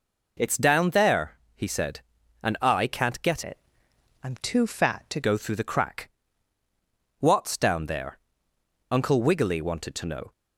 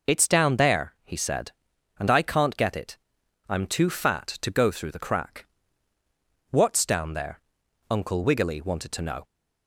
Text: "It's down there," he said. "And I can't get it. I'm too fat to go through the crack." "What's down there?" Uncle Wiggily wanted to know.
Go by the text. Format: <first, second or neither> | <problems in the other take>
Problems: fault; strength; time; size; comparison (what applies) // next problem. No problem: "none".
second | changes voice from "it" to "to"; from 3.4 to 5.2 s; 1.8 s long